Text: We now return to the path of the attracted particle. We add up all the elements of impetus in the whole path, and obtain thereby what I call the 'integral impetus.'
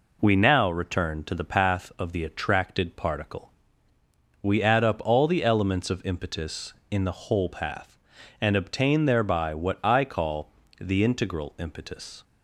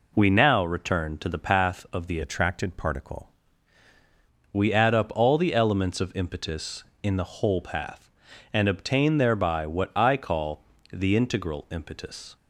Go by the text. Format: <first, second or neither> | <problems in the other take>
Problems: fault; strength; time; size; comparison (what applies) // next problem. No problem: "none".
first | changes voice from "attracted" to "particle"; from 2.2 to 3.2 s; 1.0 s long // pauses between "call" and "the"; slight; at 10.6 s; 0.30 s long; slight in the first